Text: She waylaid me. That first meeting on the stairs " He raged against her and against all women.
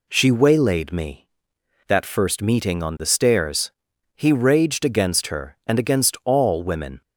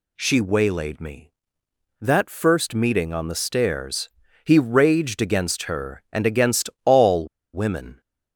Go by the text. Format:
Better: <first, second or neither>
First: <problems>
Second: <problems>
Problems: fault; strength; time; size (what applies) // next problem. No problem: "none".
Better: first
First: none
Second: pauses between "all" and "women"; slight; at 7.2 s; 0.26 s long